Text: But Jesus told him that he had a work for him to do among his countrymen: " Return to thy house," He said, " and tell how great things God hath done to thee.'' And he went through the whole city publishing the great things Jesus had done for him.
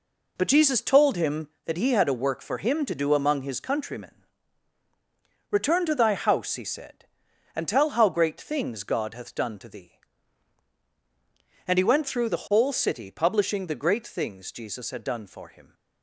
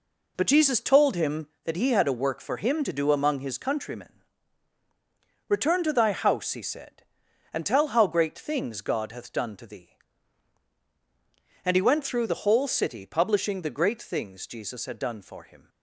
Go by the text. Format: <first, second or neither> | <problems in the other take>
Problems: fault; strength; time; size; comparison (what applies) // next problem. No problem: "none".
neither | none